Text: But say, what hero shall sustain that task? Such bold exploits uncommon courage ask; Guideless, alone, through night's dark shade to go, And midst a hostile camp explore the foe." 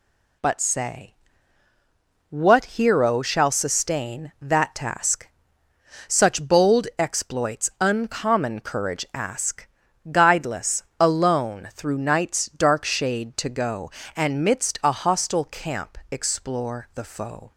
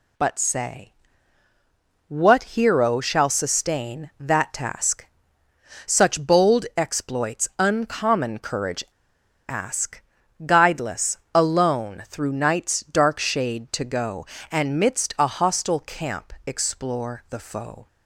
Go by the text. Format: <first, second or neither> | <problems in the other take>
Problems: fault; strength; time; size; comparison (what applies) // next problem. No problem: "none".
first | pauses between "courage" and "ask"; noticeable; at 8.8 s; 0.66 s long